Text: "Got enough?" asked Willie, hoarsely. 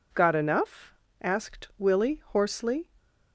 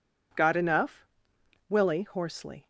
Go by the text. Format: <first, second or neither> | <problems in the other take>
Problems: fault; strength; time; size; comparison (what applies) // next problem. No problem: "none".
first | skips "asked"; at 1.3 s